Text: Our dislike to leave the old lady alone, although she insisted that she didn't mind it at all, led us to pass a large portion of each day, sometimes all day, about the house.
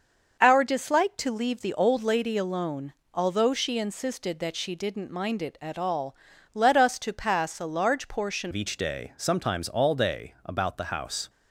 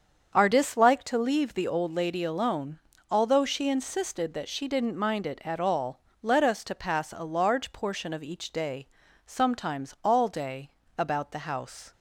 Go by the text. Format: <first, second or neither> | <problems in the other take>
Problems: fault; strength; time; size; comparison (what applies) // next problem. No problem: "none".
second | starts louder than the rest; until 1.4 s; 6.5 dB; strong in the second // changes voice at "of"; from 8.5 s on; 2.7 s long